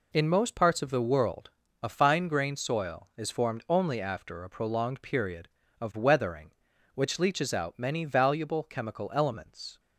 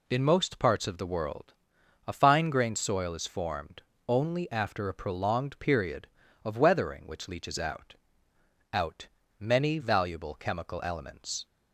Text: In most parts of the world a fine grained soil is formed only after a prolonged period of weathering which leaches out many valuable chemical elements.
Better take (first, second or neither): first